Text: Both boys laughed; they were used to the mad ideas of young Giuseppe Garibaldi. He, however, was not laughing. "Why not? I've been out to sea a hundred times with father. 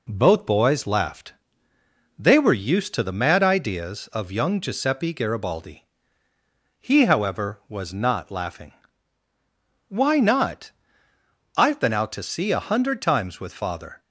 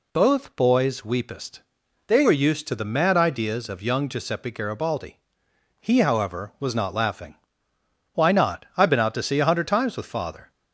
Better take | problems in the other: first | says "weepest" for "laughed"; at 1.0 s

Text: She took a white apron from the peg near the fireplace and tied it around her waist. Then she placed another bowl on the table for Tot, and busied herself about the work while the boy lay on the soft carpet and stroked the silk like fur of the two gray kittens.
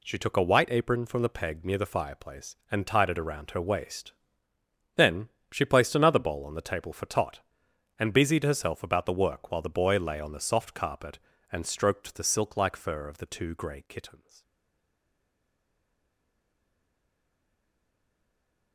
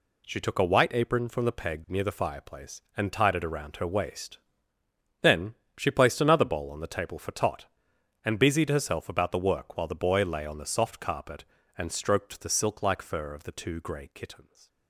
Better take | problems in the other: second | pauses between "Then" and "she"; slight; at 5.2 s; 0.24 s long; slight in the second // stays silent after the last word; strong; from 14.4 s on; 4.3 s long

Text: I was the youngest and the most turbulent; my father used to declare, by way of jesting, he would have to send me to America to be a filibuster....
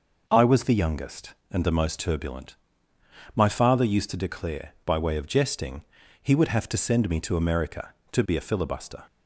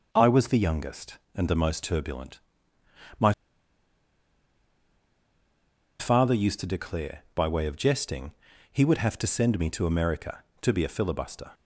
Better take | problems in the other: first | pauses between "my" and "father"; strong; at 3.3 s; 2.6 s long

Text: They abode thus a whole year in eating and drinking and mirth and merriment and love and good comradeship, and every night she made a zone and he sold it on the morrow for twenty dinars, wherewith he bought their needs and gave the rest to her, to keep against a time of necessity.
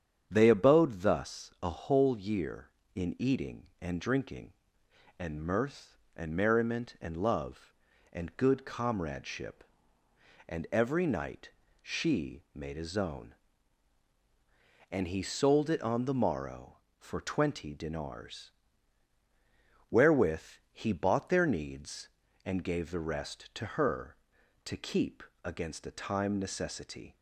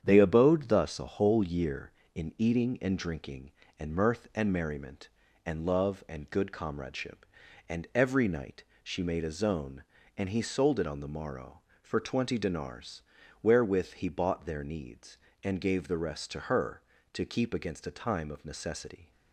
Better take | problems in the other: second | starts louder than the rest; strong; until 1.3 s; 8.5 dB; strong in the second // pauses between "night" and "she"; slight; at 11.5 s; 0.32 s long; slight in the second // pauses between "wherewith" and "he"; slight; at 20.4 s; 0.30 s long // pauses between "keep" and "against"; slight; at 25.2 s; 0.20 s long // skips "of"; at 26.3 s

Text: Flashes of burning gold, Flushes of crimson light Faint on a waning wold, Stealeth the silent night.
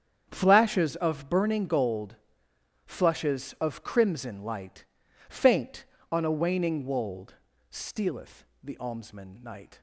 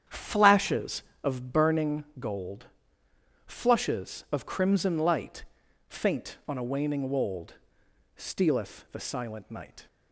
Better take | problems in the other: second | starts louder than the rest; strong; until 1.3 s; 8 dB; strong in the second // pauses between "light" and "Faint"; at 4.8 s; 0.44 s long; also in the second // pauses between "Stealeth" and "the"; slight; at 8.4 s; 0.18 s long // says "almsman" for "silent"; at 8.7 s

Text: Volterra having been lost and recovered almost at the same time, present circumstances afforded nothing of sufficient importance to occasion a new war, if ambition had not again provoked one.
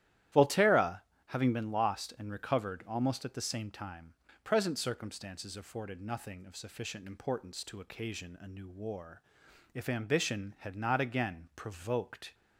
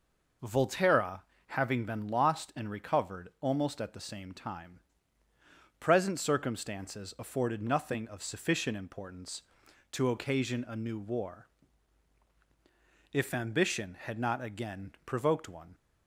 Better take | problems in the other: second | starts louder than the rest; strong; until 1.6 s; 12.5 dB // pauses between "Volterra" and "having"; slight; at 0.9 s; 0.28 s long; slight in the second // stops before "one"; at 12.3 s

